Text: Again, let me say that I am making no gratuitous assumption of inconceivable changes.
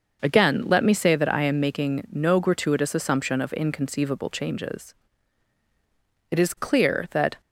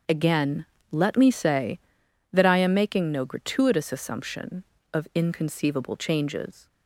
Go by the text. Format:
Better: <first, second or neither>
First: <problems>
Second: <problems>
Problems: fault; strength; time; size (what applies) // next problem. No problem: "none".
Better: second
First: starts louder than the rest; noticeable; until 1.2 s; 6 dB // goes on to say "It is clear that"; noticeable; from 6.2 s on; 1.1 s long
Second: starts louder than the rest; until 1.3 s; 7 dB